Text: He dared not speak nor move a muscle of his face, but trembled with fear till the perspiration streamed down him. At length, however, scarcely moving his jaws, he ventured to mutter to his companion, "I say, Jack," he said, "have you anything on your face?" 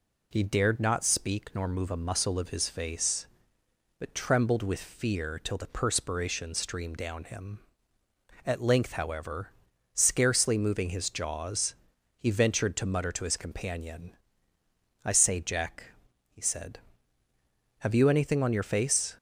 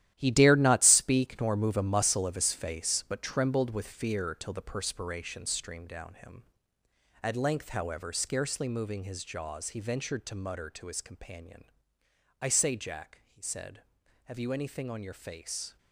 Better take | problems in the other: first | gets quieter; strong; throughout; 11 dB

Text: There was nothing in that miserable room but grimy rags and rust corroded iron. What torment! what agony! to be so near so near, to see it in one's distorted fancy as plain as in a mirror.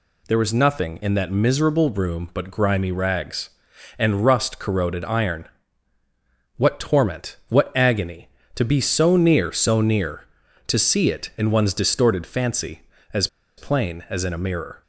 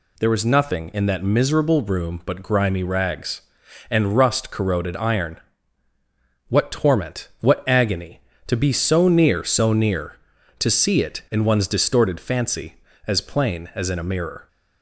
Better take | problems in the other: second | pauses between "as" and "plain"; slight; at 13.2 s; 0.29 s long

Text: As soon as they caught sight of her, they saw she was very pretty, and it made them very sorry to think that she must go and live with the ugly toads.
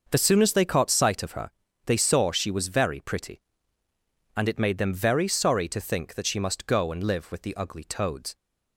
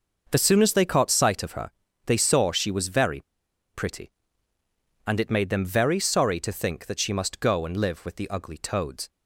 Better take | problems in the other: first | starts louder than the rest; noticeable; until 1.3 s; 6 dB; noticeable in the first // pauses between "very" and "pretty"; noticeable; at 3.2 s; 0.52 s long

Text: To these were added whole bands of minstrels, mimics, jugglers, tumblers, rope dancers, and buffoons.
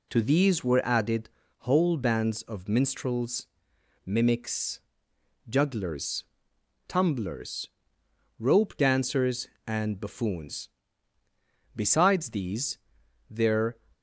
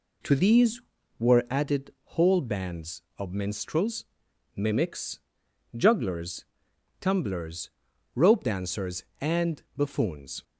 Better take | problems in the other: second | pauses between "added" and "whole"; slight; at 1.3 s; 0.28 s long // goes on to say "Besides these there"; strong; from 11.7 s on; 2.0 s long

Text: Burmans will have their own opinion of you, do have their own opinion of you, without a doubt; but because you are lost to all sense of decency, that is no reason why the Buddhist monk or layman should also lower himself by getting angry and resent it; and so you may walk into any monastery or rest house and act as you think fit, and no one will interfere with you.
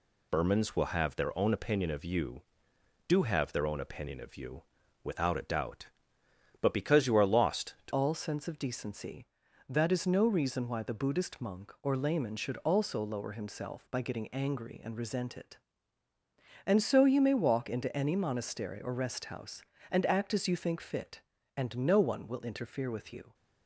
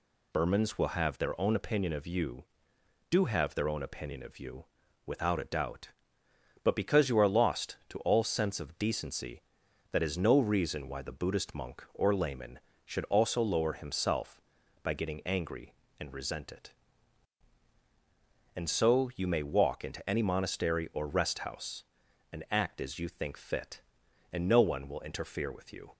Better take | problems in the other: second | changes voice at "all"; from 7.9 s on; 15.4 s long

